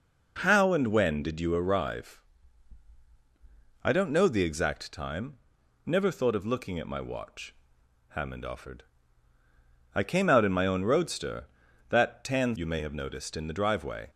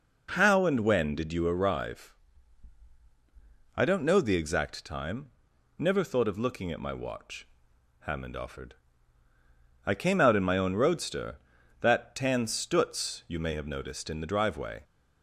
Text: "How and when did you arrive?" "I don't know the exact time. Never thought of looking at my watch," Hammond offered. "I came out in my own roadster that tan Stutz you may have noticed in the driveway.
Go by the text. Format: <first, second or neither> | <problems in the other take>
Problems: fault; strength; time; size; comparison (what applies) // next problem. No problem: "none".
second | skips "Stutz"; at 12.5 s